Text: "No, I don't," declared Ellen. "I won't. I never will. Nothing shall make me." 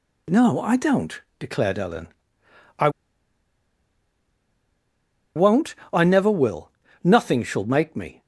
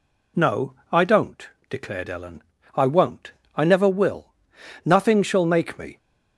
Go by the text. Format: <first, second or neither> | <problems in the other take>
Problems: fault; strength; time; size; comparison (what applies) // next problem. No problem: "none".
second | pauses between "I" and "won't"; strong; at 2.8 s; 2.4 s long